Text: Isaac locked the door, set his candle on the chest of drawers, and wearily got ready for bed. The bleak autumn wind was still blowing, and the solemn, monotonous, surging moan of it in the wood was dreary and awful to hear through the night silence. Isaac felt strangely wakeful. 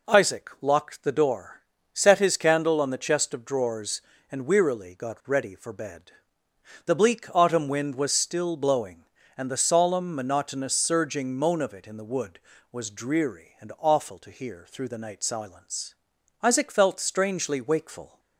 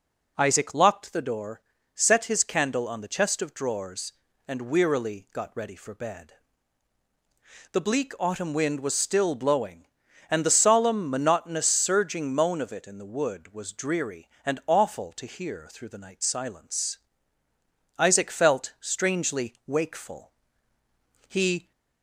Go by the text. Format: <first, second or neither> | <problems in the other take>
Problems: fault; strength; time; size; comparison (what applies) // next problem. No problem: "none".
first | goes on to say "He"; slight; from 21.2 s on; 0.44 s long